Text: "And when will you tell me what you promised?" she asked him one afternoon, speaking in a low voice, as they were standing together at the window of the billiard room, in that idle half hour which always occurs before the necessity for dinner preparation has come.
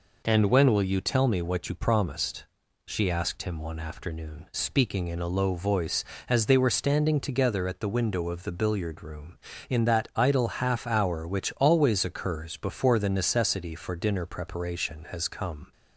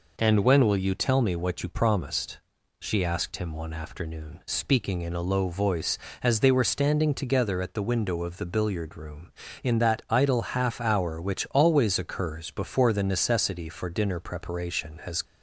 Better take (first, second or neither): first